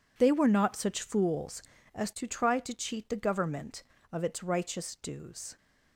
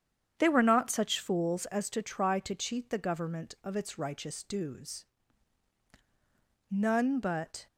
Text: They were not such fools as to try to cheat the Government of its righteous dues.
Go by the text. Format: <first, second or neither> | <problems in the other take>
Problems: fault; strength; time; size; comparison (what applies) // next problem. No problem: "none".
first | starts louder than the rest; strong; until 1.3 s; 8.5 dB // goes on to say "None but"; noticeable; from 6.6 s on; 0.98 s long